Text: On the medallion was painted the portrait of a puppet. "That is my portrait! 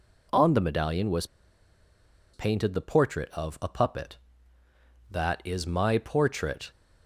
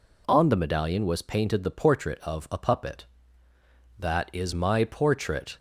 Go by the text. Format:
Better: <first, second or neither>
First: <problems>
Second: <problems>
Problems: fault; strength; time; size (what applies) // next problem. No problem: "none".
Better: second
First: pauses between "was" and "painted"; at 1.2 s; 1.0 s long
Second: none